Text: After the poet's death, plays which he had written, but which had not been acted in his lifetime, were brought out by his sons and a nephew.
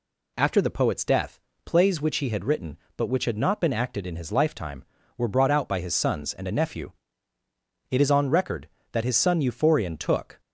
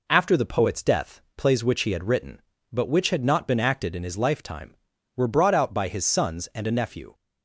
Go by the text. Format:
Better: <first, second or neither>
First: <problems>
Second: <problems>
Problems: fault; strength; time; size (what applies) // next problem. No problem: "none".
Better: second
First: goes on to say "It is on record that his son Euphorion took"; strong; from 7.9 s on; 2.4 s long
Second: none